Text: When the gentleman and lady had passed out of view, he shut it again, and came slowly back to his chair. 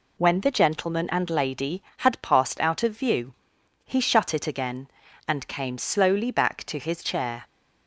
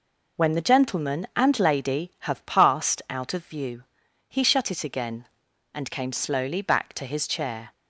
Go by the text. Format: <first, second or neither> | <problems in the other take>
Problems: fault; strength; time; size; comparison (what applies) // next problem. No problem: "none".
first | says "have" for "had"; at 2.2 s